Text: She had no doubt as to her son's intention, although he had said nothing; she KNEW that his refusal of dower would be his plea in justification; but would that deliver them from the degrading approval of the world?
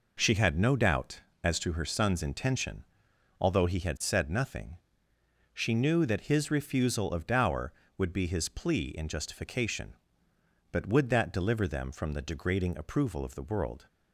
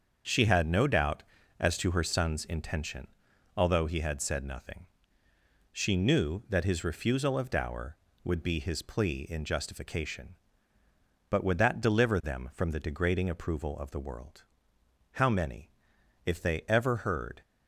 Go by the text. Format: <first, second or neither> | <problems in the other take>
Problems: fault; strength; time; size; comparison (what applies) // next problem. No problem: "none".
first | starts louder than the rest; until 1.6 s; 7 dB // goes on to say "How many if they ever heard"; strong; from 15.1 s on; 2.2 s long